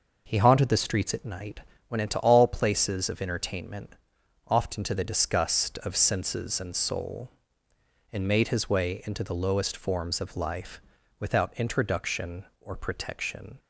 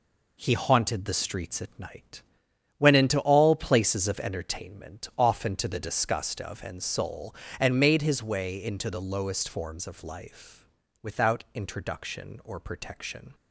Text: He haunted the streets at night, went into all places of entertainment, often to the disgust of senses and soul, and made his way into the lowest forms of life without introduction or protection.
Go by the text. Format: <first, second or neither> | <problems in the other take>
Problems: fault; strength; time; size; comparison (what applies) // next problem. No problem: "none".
first | skips "senses"; at 6.6 s // pauses between "life" and "without"; slight; at 10.6 s; 0.34 s long; also in the first